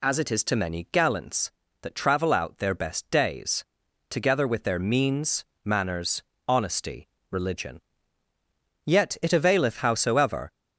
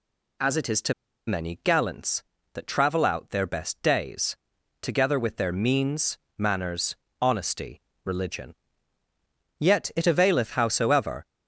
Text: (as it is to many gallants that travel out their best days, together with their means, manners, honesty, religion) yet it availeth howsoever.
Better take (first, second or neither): first